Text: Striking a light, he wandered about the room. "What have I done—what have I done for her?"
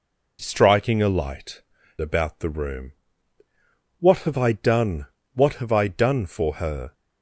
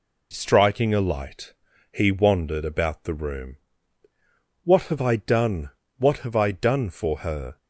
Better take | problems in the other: second | skips "he wandered"; at 1.7 s

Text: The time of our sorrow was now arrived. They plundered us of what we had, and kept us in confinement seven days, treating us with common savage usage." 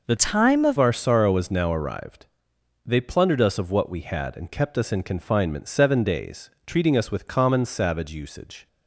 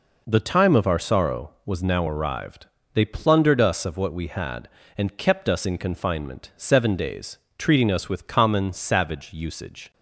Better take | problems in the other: second | changes voice from "time" to "of"; from 0.1 to 0.7 s; 0.6 s long

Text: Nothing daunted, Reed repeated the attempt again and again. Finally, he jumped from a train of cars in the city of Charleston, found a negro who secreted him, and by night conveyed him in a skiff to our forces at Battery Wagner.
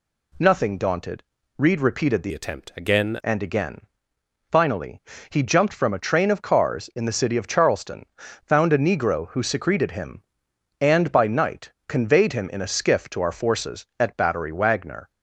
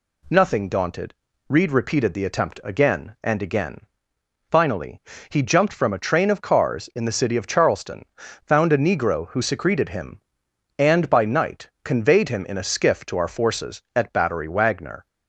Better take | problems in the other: second | changes voice from "attempt" to "again"; from 2.3 to 3.1 s; 0.8 s long // pauses between "night" and "conveyed"; slight; at 11.7 s; 0.16 s long

